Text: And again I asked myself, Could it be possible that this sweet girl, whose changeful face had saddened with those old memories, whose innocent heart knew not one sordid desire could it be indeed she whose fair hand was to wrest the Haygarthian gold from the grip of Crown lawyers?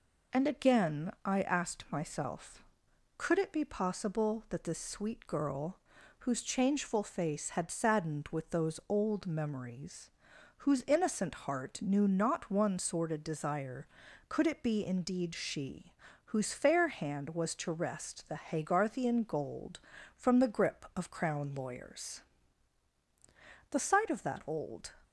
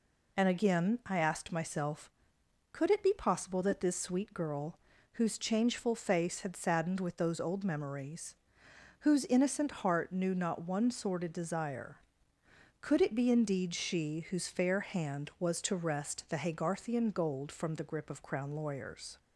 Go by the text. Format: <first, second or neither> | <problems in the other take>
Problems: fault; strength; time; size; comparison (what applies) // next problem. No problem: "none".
second | pauses between "she" and "whose"; at 15.9 s; 0.38 s long // goes on to say "The sight of that old"; noticeable; from 23.7 s on; 1.2 s long